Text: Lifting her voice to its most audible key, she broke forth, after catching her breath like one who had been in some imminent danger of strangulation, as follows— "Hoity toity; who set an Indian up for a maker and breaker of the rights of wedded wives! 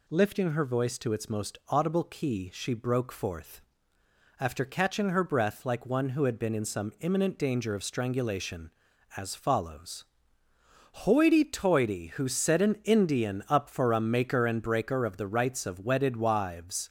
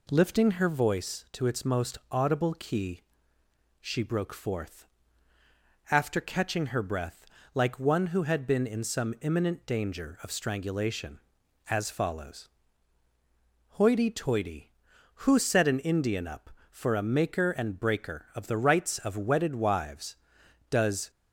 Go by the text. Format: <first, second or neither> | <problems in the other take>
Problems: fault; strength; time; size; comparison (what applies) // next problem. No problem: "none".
first | pauses between "breath" and "like"; slight; at 7.2 s; 0.28 s long // goes on to say "Does"; slight; from 20.6 s on; 0.40 s long